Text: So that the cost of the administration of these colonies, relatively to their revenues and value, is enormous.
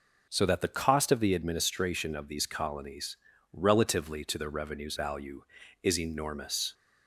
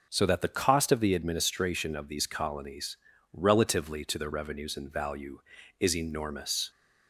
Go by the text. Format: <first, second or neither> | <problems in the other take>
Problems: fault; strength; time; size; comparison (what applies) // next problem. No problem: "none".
second | skips "and"; at 4.9 s